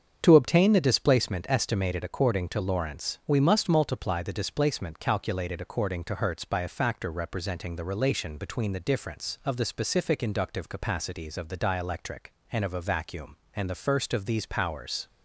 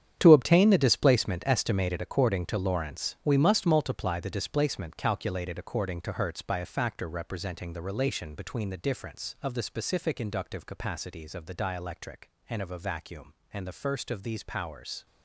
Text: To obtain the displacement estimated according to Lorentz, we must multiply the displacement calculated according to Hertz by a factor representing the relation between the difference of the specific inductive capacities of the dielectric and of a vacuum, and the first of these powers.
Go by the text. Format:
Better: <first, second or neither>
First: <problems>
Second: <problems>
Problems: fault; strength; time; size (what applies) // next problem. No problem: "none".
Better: first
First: starts louder than the rest; strong; until 1.2 s; 7 dB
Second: gets quieter; strong; throughout; 12 dB // starts louder than the rest; strong; until 1.1 s; 9 dB